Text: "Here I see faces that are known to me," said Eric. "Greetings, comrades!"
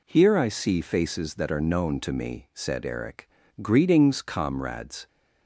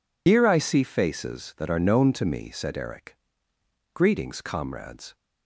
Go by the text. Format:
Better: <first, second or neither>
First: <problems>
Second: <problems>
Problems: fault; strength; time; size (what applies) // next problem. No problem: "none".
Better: first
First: none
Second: loses the start of "Here"; at 0.2 s; 80 ms